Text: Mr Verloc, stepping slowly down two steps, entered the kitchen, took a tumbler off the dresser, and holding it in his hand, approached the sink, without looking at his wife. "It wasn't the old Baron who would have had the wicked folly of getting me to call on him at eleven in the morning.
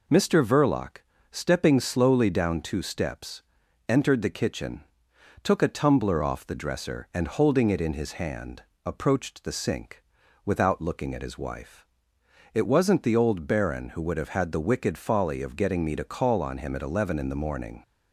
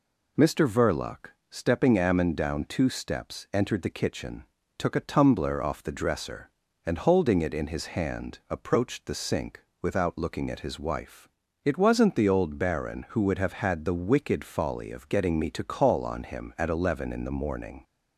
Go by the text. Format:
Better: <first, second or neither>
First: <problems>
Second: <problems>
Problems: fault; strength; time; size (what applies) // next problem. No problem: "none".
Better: first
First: none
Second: says "ammon" for "slowly"; at 1.9 s